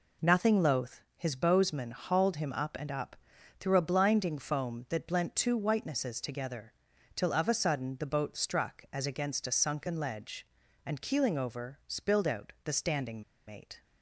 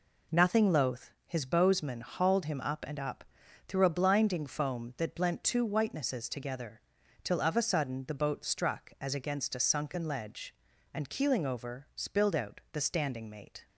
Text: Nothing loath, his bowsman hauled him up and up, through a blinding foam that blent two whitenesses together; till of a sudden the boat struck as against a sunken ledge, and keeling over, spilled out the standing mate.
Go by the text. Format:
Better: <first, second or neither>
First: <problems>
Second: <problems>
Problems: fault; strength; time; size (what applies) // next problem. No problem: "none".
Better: second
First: pauses between "standing" and "mate"; slight; at 13.2 s; 0.26 s long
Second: none